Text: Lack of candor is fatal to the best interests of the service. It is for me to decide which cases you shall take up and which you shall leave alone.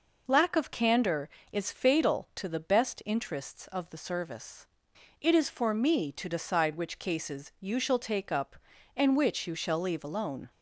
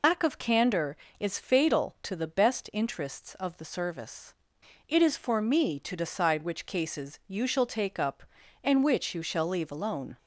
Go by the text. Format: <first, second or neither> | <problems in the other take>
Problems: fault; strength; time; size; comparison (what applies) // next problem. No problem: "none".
first | loses the start of "Lack"; at 0.0 s; 85 ms